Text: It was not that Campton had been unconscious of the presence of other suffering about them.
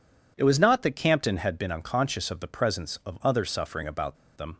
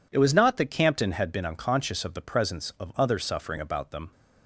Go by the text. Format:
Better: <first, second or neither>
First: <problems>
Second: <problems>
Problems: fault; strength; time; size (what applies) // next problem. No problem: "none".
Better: second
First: pauses between "about" and "them"; slight; at 4.1 s; 0.21 s long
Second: none